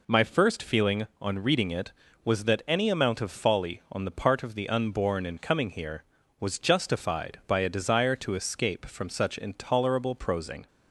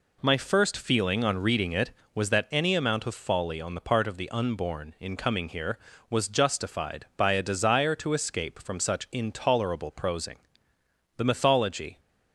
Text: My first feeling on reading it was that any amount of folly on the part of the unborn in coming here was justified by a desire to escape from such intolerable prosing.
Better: first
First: none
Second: goes on to say "The mythology"; noticeable; from 11.1 s on; 0.84 s long

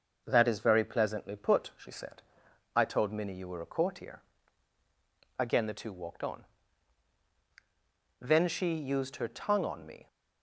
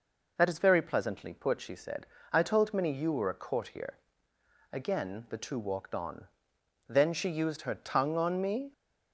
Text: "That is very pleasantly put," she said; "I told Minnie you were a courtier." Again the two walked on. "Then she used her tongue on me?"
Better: neither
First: none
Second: none

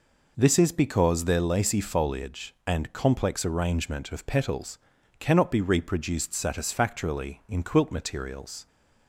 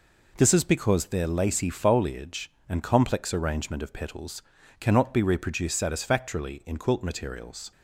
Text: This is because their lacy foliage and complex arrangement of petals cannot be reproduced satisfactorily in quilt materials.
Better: neither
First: pauses between "petals" and "cannot"; at 4.7 s; 0.42 s long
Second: pauses between "petals" and "cannot"; at 4.4 s; 0.40 s long

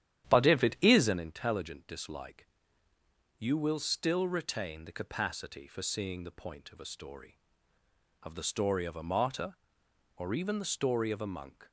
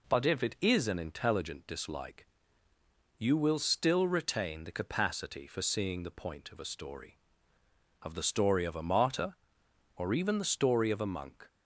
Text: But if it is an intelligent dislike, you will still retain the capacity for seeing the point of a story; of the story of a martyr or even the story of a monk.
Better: second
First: starts louder than the rest; strong; until 1.2 s; 11 dB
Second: none

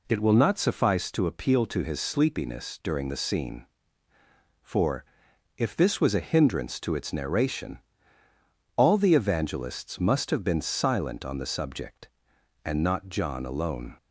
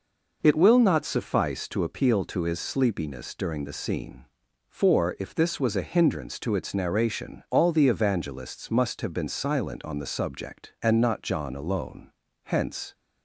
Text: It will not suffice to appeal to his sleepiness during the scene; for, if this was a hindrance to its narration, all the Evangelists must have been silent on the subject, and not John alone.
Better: first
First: none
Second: goes on to say "Hence"; from 12.4 s on; 0.50 s long

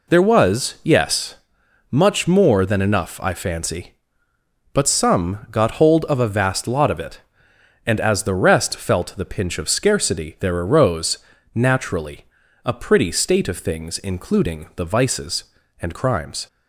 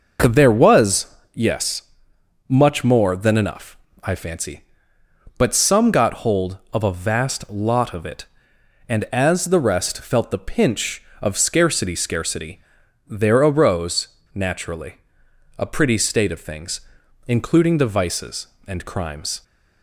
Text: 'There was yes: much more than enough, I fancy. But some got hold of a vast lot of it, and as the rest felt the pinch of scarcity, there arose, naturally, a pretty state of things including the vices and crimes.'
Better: first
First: none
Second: pauses between "was" and "yes"; slight; at 1.1 s; 0.18 s long // says "scarcity" twice; at 11.9 s // pauses between "things" and "including"; noticeable; at 16.7 s; 0.46 s long

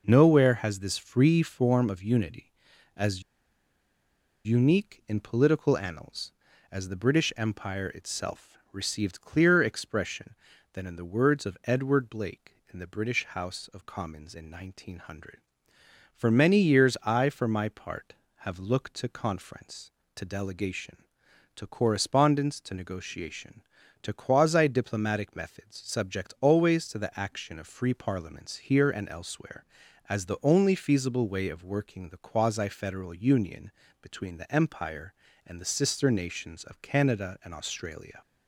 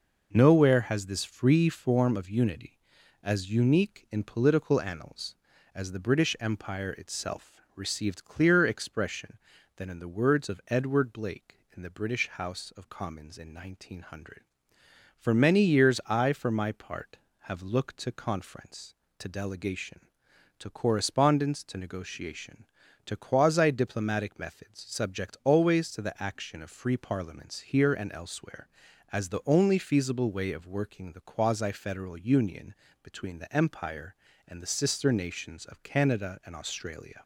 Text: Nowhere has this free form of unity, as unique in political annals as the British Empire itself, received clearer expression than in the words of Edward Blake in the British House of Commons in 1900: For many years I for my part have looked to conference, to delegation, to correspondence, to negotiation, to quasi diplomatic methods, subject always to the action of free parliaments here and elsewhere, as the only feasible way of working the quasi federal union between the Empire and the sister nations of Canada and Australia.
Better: second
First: pauses between "as" and "unique"; at 3.2 s; 1.2 s long // pauses between "union" and "between"; slight; at 33.7 s; 0.30 s long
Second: pauses between "union" and "between"; slight; at 32.7 s; 0.28 s long

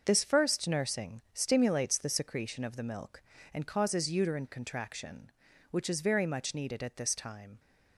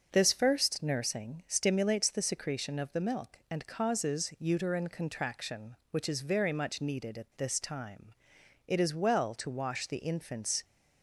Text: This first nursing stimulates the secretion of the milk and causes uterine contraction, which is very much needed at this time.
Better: first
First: starts louder than the rest; until 1.0 s; 6 dB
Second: starts louder than the rest; until 1.1 s; 6.5 dB // goes on to say "It is well to wash the infant's"; strong; from 8.6 s on; 1.9 s long

